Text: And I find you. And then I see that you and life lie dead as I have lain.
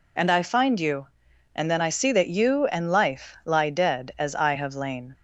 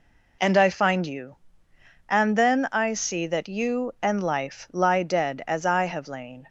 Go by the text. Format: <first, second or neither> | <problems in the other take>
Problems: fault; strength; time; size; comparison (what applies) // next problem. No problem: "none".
neither | none